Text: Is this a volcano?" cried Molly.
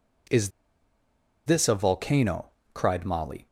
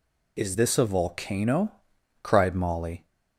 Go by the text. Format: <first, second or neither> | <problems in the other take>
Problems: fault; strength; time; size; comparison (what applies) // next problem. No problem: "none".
second | pauses between "Is" and "this"; noticeable; at 0.4 s; 0.96 s long